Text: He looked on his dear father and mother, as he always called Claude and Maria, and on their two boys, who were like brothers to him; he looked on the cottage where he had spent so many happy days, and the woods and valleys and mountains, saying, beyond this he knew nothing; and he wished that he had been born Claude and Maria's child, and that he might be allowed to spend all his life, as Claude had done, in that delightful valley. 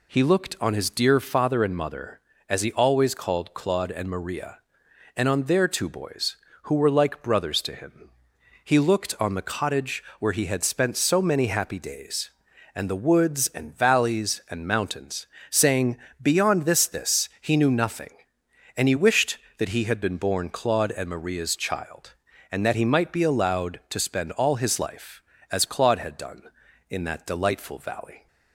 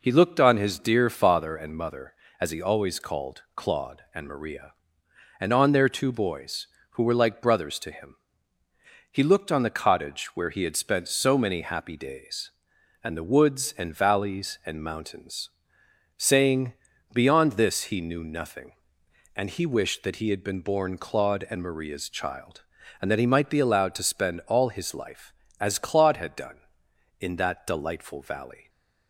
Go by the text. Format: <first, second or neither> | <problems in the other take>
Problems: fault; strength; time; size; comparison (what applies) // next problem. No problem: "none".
second | pauses between "cottage" and "where"; slight; at 10.0 s; 0.16 s long // says "this" twice; at 16.8 s